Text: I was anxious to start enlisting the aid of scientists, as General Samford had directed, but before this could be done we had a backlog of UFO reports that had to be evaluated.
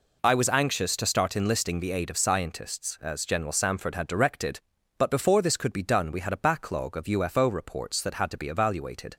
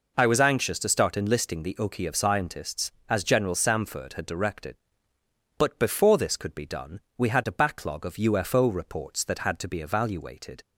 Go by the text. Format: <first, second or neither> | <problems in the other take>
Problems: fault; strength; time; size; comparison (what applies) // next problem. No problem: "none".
first | says "oki" for "aid"; at 1.7 s // pauses between "done" and "we"; slight; at 6.9 s; 0.16 s long